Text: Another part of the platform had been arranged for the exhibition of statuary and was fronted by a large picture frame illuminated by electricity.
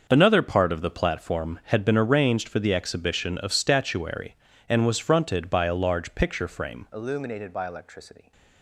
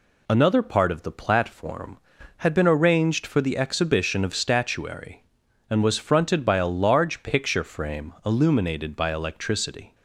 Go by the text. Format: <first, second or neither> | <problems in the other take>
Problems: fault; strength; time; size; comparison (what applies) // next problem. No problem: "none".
second | starts louder than the rest; until 1.1 s; 6.5 dB // changes voice at "illuminated"; from 6.9 s on; 1.4 s long